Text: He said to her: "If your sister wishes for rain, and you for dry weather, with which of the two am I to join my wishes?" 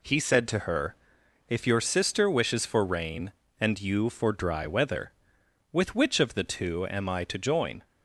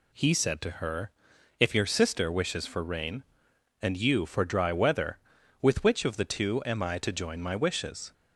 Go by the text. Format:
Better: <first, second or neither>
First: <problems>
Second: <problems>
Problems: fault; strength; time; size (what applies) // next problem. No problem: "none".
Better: second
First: stops before "my wishes"; at 7.8 s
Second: none